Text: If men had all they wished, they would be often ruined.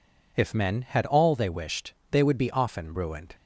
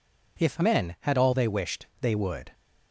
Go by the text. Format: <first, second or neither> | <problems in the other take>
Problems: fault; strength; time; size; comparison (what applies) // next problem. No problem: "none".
first | stops before "be often ruined"; at 2.5 s